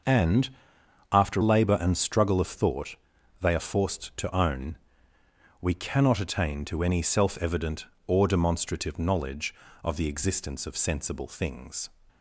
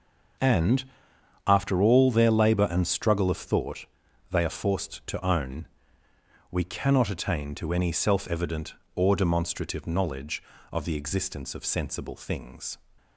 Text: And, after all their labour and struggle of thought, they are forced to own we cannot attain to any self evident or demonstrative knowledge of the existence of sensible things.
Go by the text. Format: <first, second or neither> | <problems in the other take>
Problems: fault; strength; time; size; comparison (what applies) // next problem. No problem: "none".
second | starts louder than the rest; noticeable; until 1.6 s; 6 dB; also in the second // skips "all their"; at 1.4 s // pauses between "own" and "we"; noticeable; at 4.7 s; 0.86 s long; noticeable in the second